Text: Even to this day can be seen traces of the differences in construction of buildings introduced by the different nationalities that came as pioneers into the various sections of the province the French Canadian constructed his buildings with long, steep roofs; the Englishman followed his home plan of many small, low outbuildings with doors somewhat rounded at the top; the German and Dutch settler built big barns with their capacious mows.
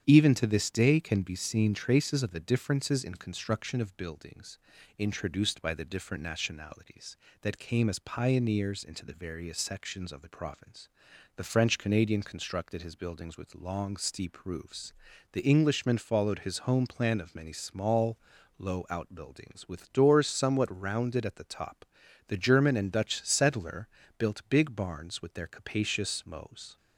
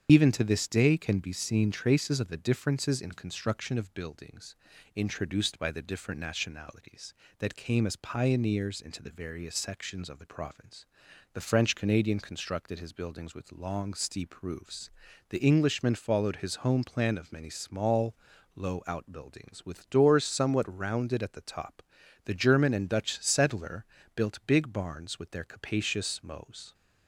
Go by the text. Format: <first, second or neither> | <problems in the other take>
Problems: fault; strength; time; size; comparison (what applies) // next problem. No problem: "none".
first | loses the start of "Even"; at 0.0 s; 60 ms // starts louder than the rest; strong; until 1.1 s; 8.5 dB; strong in the first // pauses between "buildings" and "introduced"; at 4.5 s; 0.40 s long; also in the first // pauses between "province" and "the"; noticeable; at 10.8 s; 0.48 s long; noticeable in the first // pauses between "settler" and "built"; slight; at 23.8 s; 0.30 s long; slight in the first